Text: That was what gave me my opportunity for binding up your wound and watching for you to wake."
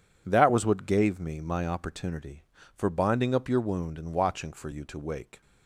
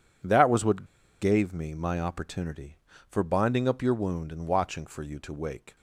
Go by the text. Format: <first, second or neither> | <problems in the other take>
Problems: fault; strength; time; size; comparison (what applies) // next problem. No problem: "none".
first | pauses between "what" and "gave"; at 0.8 s; 0.36 s long